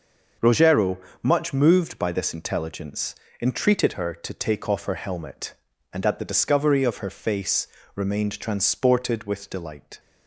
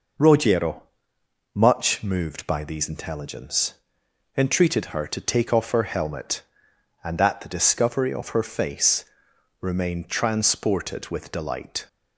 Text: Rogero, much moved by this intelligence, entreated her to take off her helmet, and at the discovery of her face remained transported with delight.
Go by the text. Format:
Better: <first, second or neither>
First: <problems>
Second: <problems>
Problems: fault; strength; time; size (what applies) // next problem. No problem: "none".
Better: first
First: pauses between "face" and "remained"; slight; at 7.6 s; 0.30 s long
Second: says "these" for "this"; at 2.6 s // pauses between "face" and "remained"; noticeable; at 9.0 s; 0.56 s long